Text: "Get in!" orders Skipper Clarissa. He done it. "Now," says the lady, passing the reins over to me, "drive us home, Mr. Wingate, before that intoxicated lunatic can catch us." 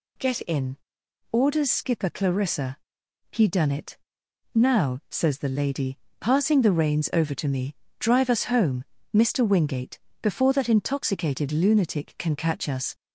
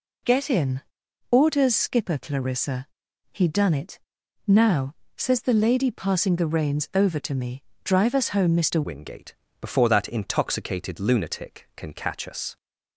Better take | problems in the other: first | changes voice at "Wingate"; from 8.8 s on; 3.7 s long

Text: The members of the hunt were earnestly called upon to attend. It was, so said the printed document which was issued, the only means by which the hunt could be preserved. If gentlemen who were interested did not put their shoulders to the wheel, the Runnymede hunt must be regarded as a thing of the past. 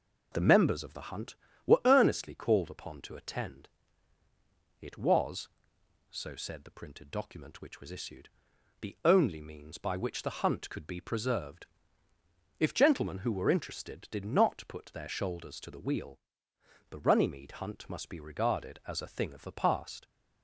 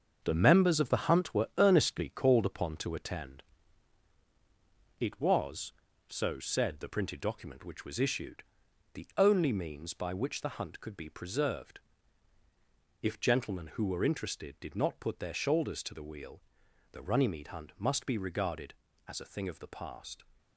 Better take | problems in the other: first | gets quieter; strong; throughout; 7.5 dB

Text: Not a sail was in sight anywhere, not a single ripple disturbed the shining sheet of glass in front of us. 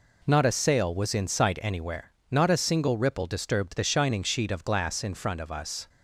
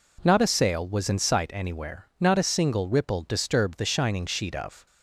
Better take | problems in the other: first | stops before "glass in front of us"; at 4.8 s

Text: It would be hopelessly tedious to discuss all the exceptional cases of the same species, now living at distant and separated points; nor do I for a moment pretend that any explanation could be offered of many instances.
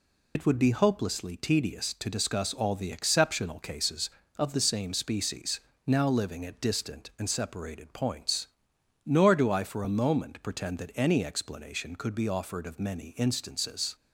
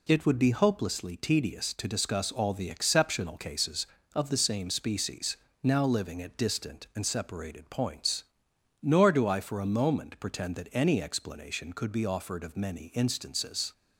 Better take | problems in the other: second | loses the start of "It"; at 0.3 s; 85 ms

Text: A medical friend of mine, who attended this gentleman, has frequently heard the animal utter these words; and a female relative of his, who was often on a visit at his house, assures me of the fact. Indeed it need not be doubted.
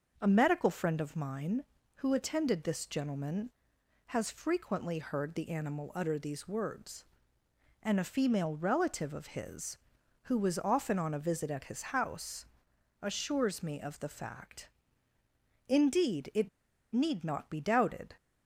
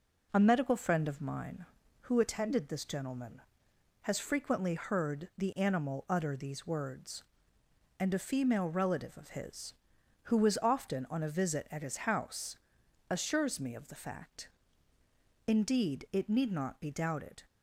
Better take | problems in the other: second | starts louder than the rest; until 1.2 s; 6 dB // pauses between "it" and "need"; at 16.4 s; 0.43 s long

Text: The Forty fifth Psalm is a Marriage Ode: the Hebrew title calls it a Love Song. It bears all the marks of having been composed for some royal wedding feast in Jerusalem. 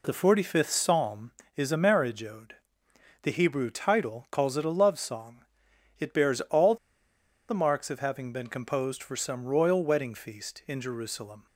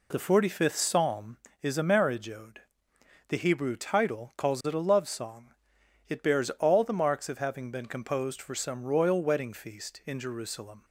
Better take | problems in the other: second | pauses between "all" and "the"; noticeable; at 6.7 s; 0.73 s long

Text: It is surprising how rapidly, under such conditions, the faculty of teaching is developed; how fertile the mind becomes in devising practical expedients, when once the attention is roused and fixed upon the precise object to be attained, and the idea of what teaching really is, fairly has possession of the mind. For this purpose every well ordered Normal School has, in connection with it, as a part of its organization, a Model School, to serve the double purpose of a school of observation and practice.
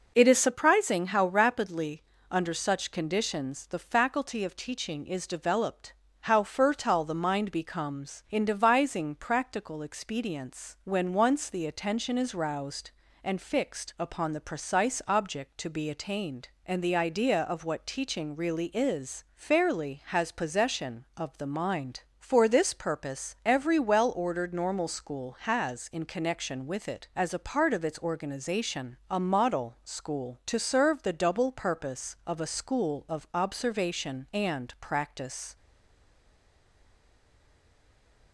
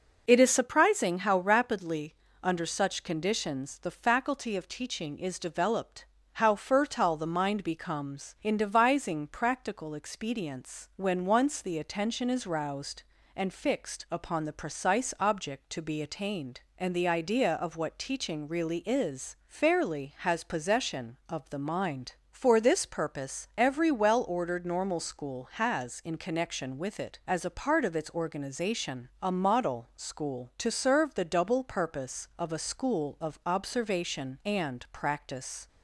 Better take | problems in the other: second | stays silent after the last word; strong; from 35.5 s on; 2.8 s long

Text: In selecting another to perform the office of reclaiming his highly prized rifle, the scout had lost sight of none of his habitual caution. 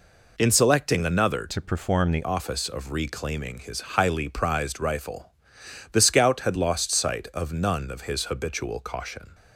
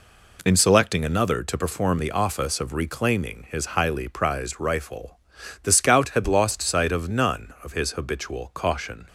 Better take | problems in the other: second | changes voice from "to" to "the"; from 1.4 to 2.2 s; 0.8 s long // pauses between "his" and "highly"; slight; at 3.7 s; 0.16 s long

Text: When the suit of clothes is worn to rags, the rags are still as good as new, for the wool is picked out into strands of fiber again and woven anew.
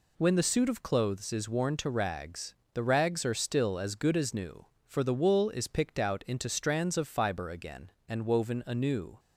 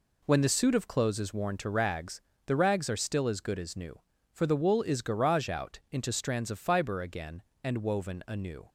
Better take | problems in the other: first | says "garage" for "picked"; at 5.0 s

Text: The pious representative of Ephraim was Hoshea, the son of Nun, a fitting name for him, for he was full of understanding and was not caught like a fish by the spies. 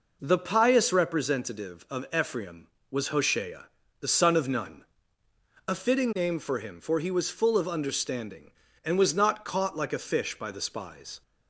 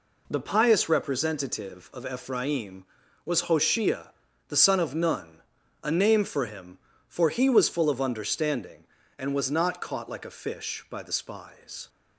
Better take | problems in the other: first | skips "fitting"; at 5.9 s

